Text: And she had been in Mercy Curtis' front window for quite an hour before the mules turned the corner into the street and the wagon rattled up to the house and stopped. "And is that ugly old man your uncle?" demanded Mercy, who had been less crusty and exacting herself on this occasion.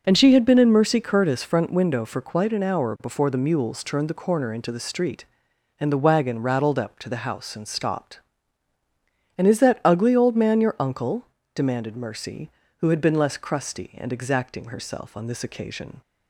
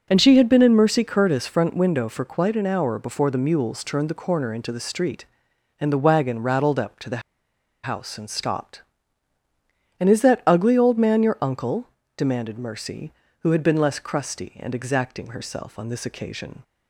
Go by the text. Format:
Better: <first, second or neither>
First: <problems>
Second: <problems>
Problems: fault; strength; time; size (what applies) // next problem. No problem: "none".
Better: first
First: none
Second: pauses between "the" and "house"; noticeable; at 7.2 s; 0.62 s long